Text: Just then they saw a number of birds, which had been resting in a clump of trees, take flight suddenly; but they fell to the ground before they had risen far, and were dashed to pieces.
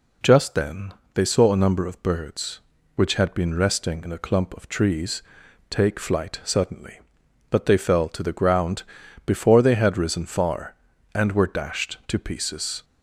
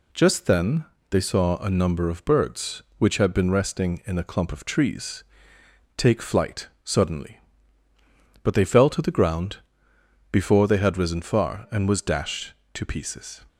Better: first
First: pauses between "then" and "they"; slight; at 0.9 s; 0.20 s long // pauses between "ground" and "before"; at 8.8 s; 0.42 s long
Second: pauses between "then" and "they"; slight; at 0.8 s; 0.26 s long // pauses between "flight" and "suddenly"; slight; at 6.6 s; 0.16 s long // pauses between "ground" and "before"; noticeable; at 9.5 s; 0.74 s long // says "was" for "were"; at 11.8 s

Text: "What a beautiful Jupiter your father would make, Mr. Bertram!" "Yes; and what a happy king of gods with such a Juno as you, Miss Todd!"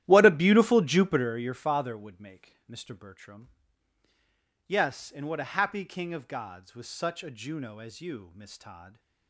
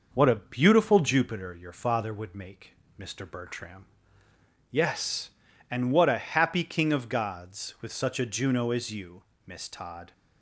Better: second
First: starts louder than the rest; strong; until 1.4 s; 12.5 dB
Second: none

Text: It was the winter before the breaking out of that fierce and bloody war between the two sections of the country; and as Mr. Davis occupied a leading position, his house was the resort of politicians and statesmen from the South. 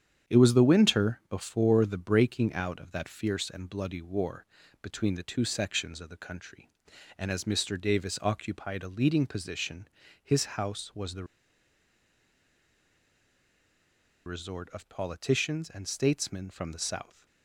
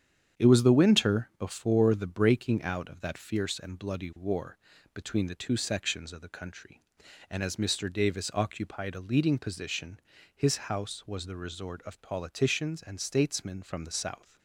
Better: second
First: starts louder than the rest; strong; until 1.3 s; 8.5 dB // pauses between "war" and "between"; at 4.4 s; 0.38 s long // pauses between "the" and "resort"; strong; at 11.2 s; 3.0 s long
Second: starts louder than the rest; strong; until 1.4 s; 8.5 dB // pauses between "war" and "between"; at 4.5 s; 0.38 s long

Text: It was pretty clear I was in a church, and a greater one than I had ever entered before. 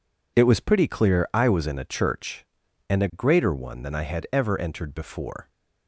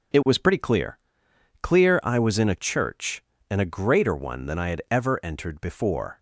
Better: first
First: none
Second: says "clear" twice; at 1.6 s

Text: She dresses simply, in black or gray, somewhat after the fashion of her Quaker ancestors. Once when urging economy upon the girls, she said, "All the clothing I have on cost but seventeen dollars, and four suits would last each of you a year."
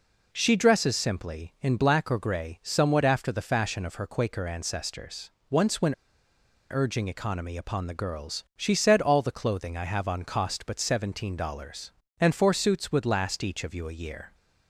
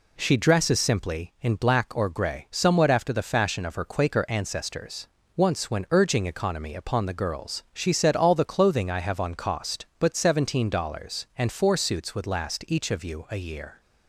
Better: second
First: pauses between "when" and "urging"; noticeable; at 5.9 s; 0.78 s long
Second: none

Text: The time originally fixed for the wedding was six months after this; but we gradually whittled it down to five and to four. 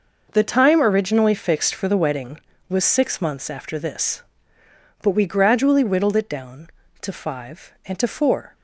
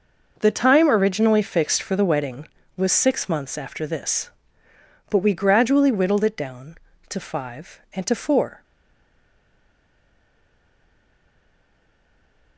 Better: first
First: none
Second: stays silent after the last word; strong; from 8.6 s on; 3.9 s long

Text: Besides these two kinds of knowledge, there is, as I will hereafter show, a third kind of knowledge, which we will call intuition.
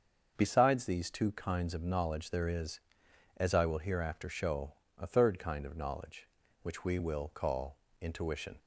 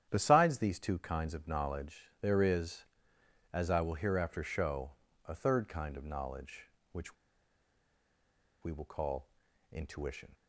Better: first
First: starts louder than the rest; until 1.3 s; 6.5 dB // pauses between "call" and "intuition"; slight; at 7.7 s; 0.24 s long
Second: starts louder than the rest; strong; until 1.1 s; 10 dB // pauses between "which" and "we"; strong; at 7.1 s; 1.4 s long // pauses between "call" and "intuition"; at 9.2 s; 0.44 s long

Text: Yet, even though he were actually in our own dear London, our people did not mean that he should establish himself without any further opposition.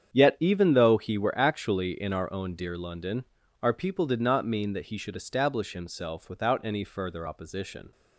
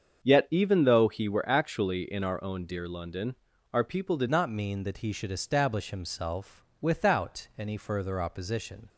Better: first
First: starts louder than the rest; strong; until 1.1 s; 8 dB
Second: starts louder than the rest; until 1.2 s; 7 dB // changes voice at "not"; from 4.2 s on; 4.6 s long // pauses between "himself" and "without"; slight; at 6.6 s; 0.16 s long

